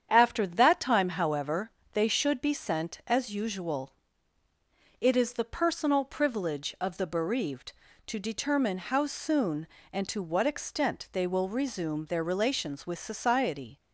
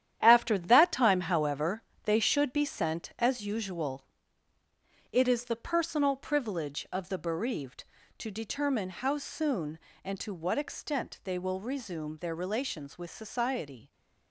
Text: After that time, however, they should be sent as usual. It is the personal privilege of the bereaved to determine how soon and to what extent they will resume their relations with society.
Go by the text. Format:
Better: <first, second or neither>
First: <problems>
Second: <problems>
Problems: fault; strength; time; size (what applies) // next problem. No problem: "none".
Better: first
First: starts louder than the rest; strong; until 1.1 s; 8.5 dB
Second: gets quieter; strong; throughout; 9.5 dB // starts louder than the rest; strong; until 1.2 s; 10.5 dB